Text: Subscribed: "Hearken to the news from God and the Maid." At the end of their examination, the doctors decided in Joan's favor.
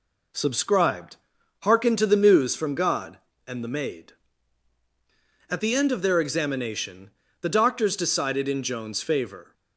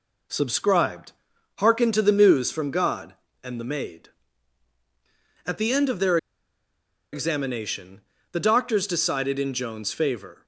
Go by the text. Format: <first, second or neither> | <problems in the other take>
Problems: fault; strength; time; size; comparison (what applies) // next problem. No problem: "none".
first | pauses between "their" and "examination"; noticeable; at 6.1 s; 0.95 s long